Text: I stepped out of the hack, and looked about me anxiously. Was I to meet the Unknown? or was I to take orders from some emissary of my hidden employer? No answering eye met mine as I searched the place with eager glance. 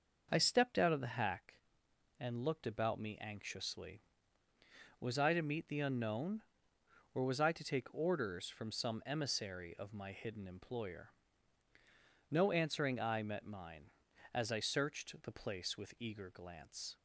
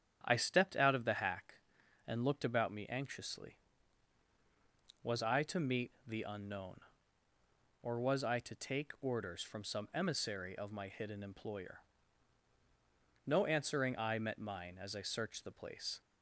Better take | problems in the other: first | starts louder than the rest; strong; until 1.2 s; 8.5 dB; noticeable in the first // pauses between "meet" and "the"; slight; at 5.8 s; 0.16 s long // stops before "with eager glance"; at 15.9 s

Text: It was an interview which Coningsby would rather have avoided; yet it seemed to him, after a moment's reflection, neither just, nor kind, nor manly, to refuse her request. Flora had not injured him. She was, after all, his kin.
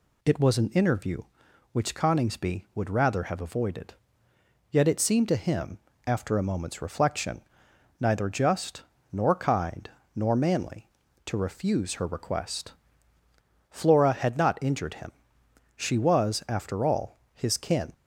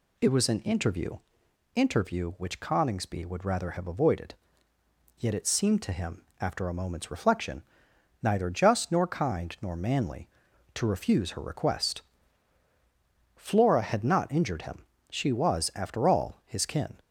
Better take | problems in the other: first | says "interview" twice; at 1.7 s

